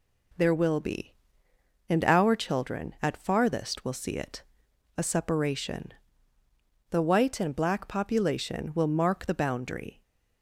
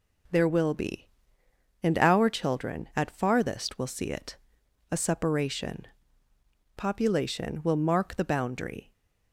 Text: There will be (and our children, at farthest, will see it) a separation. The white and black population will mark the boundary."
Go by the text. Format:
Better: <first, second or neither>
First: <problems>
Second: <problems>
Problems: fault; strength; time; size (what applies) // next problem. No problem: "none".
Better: first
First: none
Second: skips "The white and black"; at 6.3 s